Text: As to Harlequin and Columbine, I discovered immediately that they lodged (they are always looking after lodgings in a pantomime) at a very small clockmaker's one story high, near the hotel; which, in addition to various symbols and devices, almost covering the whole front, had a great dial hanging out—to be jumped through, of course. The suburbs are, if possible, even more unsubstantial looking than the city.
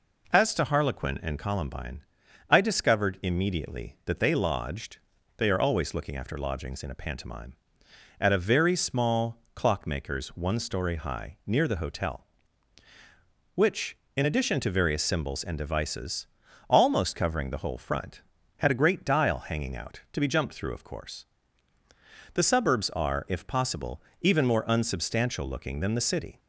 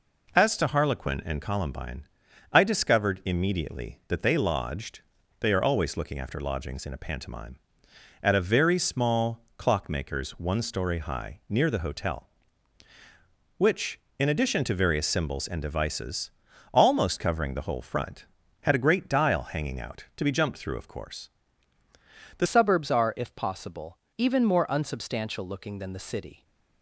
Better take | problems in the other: first | pauses between "small" and "clockmaker's"; slight; at 9.4 s; 0.16 s long; slight in the first // changes voice at "suburbs"; from 22.4 s on; 4.0 s long

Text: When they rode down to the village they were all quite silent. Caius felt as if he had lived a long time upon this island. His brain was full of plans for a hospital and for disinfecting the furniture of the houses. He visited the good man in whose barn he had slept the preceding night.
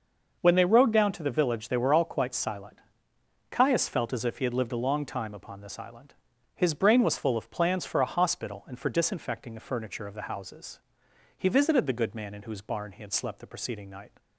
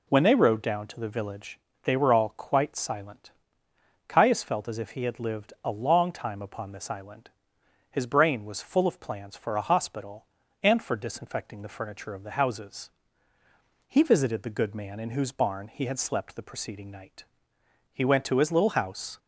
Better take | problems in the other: first | pauses between "village" and "they"; slight; at 1.5 s; 0.24 s long // goes on to say "He went to his little house"; noticeable; from 17.9 s on; 1.2 s long

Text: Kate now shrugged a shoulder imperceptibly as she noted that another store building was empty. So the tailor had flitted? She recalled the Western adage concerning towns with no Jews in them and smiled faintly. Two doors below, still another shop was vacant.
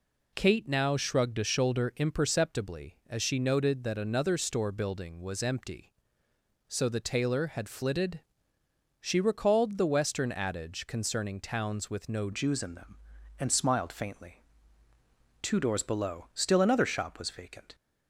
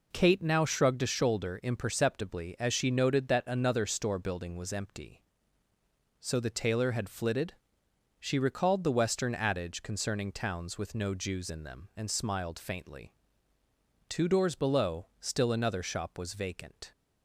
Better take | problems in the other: second | changes voice at "Jews"; from 12.3 s on; 5.4 s long

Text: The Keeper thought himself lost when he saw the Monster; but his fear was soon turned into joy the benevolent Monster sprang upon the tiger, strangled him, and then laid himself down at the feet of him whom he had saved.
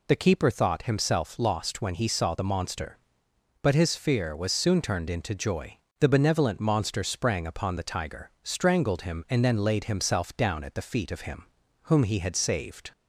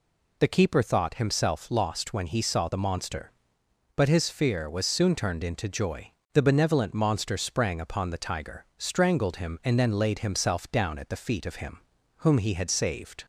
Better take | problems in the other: neither | pauses between "joy" and "the"; slight; the same in both // pauses between "him" and "whom"; the same in both

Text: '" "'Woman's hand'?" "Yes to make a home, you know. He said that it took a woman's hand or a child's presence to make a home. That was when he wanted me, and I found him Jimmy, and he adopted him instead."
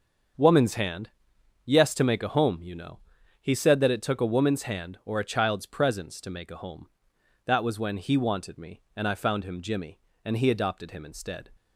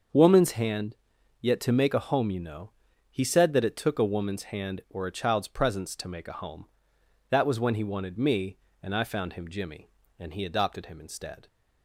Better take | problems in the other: first | starts louder than the rest; until 1.5 s; 6.5 dB; also in the first // says "Yet" for "Yes"; at 1.4 s

